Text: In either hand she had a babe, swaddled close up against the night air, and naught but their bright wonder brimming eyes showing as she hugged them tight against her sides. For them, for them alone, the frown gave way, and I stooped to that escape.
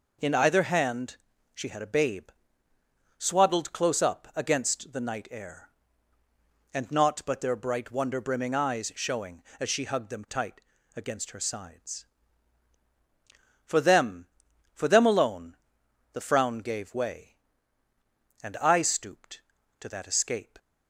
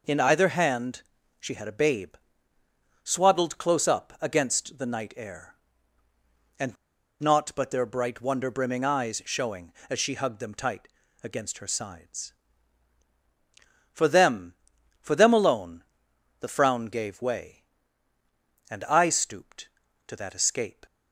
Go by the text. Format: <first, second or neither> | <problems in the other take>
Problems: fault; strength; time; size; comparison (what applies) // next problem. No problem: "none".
first | pauses between "hand" and "she"; at 1.0 s; 0.38 s long; also in the first // pauses between "and" and "naught"; noticeable; at 6.7 s; 0.46 s long // pauses between "tight" and "against"; slight; at 10.8 s; 0.36 s long; slight in the first